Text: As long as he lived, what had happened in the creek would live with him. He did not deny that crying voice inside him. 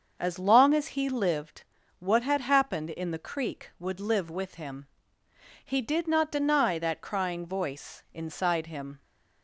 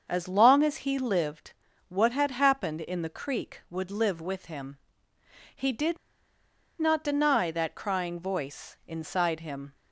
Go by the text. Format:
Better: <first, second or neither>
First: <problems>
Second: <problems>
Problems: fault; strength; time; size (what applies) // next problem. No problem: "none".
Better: first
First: starts louder than the rest; until 1.2 s; 6.5 dB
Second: starts louder than the rest; until 1.1 s; 6.5 dB // pauses between "did" and "not"; noticeable; at 5.9 s; 0.81 s long